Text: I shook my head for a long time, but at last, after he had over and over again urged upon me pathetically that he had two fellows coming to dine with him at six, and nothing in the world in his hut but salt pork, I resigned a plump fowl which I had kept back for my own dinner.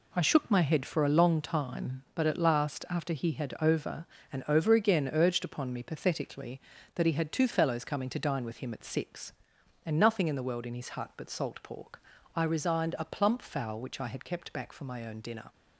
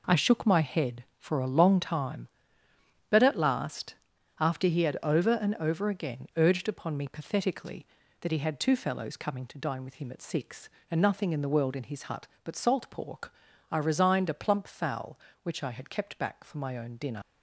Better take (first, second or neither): first